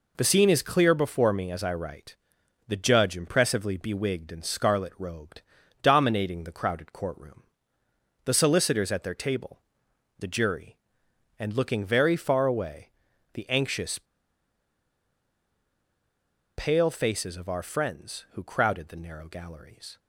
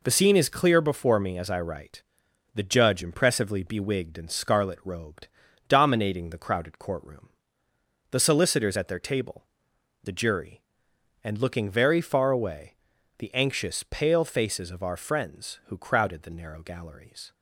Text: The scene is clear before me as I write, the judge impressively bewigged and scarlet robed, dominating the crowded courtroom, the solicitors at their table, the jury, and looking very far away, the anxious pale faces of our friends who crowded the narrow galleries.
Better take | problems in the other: second | pauses between "anxious" and "pale"; strong; at 13.9 s; 2.5 s long

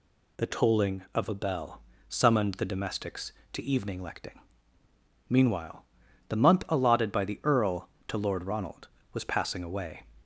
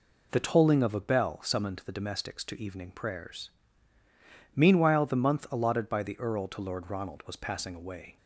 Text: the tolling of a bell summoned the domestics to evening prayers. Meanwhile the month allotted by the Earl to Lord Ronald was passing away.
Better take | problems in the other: second | pauses between "bell" and "summoned"; slight; at 1.7 s; 0.28 s long // says "lecting" for "prayers"; at 4.0 s // pauses between "Meanwhile" and "the"; at 5.8 s; 0.44 s long

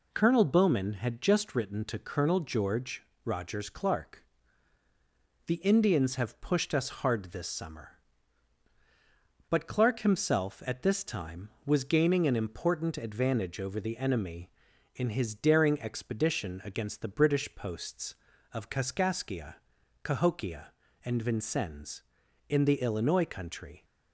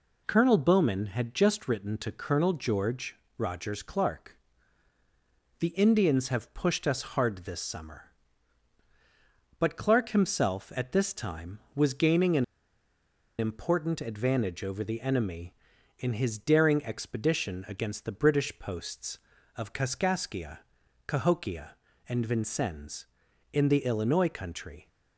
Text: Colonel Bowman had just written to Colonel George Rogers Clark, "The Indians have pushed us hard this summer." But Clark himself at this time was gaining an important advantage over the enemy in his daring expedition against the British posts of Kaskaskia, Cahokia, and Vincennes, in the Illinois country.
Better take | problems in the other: first | pauses between "George" and "Rogers"; slight; at 3.1 s; 0.20 s long; slight in the first // pauses between "an" and "important"; noticeable; at 12.4 s; 0.95 s long

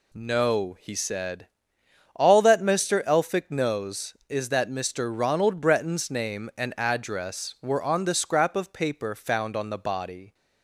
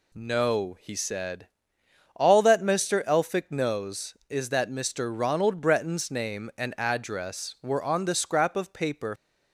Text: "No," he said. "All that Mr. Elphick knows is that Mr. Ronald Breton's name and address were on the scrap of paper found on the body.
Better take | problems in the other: first | stops before "found on the body"; at 9.1 s

